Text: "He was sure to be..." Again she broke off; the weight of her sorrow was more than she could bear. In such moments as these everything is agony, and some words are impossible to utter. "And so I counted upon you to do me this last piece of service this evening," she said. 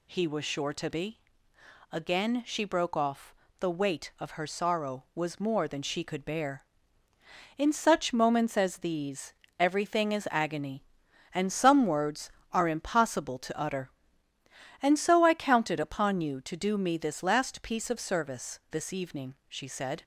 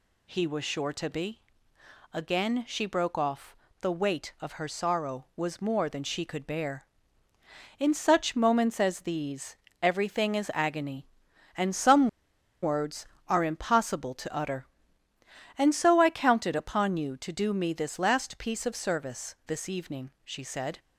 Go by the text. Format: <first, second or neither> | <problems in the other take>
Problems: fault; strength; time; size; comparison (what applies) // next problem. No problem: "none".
first | pauses between "these" and "everything"; slight; at 9.5 s; 0.26 s long; slight in the first // pauses between "some" and "words"; noticeable; at 12.0 s; 0.53 s long